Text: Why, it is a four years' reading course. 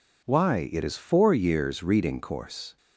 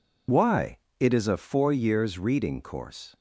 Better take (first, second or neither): second